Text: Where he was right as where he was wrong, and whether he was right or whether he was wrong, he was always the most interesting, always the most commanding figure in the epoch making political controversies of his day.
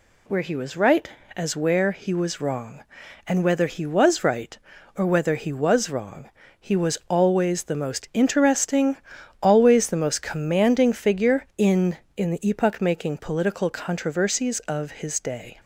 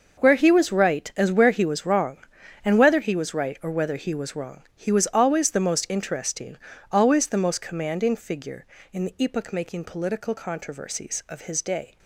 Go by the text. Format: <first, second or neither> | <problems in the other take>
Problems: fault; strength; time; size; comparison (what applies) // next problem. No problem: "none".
second | says "in" twice; at 12.1 s